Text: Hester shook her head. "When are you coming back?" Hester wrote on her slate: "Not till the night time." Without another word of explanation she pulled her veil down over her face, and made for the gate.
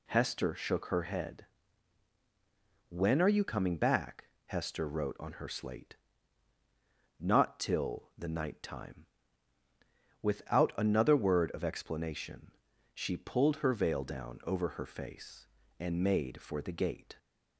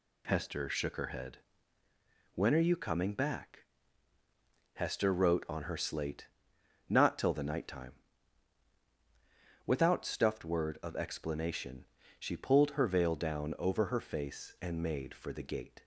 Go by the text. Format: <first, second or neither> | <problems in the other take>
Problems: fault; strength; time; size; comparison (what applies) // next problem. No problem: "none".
first | says "stuffed" for "another"; at 10.0 s // pauses between "explanation" and "she"; slight; at 11.8 s; 0.32 s long; also in the first